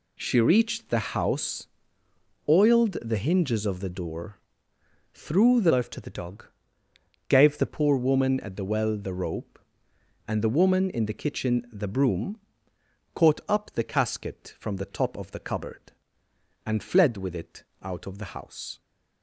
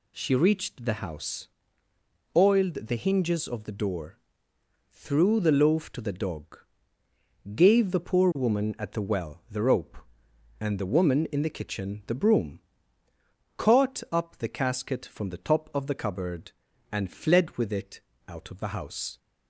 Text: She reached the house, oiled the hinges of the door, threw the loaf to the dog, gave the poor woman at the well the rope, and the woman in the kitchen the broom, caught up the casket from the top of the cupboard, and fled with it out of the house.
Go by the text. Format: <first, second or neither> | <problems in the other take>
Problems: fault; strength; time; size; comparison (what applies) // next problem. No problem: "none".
second | changes voice from "loaf" to "the"; from 5.6 to 7.6 s; 2.0 s long // pauses between "it" and "out"; slight; at 17.6 s; 0.18 s long; slight in the second